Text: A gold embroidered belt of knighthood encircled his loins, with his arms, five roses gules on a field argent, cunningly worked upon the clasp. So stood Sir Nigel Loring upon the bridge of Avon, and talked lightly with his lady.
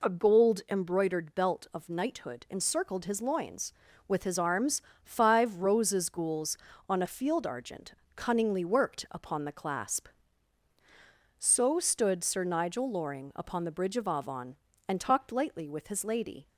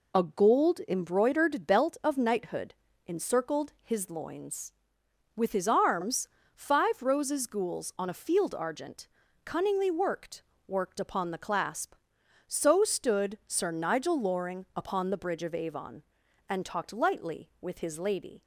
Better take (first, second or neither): first